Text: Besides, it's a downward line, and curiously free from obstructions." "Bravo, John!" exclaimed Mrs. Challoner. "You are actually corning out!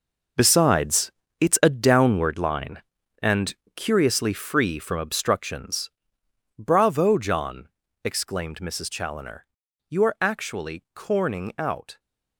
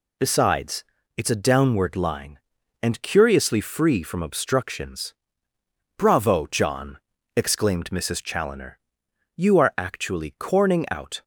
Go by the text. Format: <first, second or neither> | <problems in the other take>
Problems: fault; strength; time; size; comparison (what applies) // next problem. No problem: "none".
second | gets quieter; strong; throughout; 12 dB // pauses between "and" and "curiously"; slight; at 3.5 s; 0.22 s long